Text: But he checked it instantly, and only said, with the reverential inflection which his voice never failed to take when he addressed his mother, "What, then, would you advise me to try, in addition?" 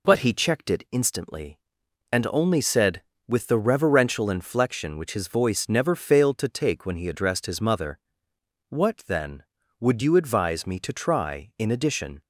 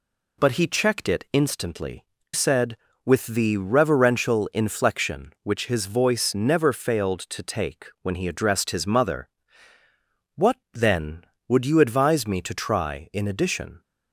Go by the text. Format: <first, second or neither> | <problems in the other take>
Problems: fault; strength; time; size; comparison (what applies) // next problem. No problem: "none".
first | skips "and only"; at 2.1 s // pauses between "take" and "when"; slight; at 7.8 s; 0.16 s long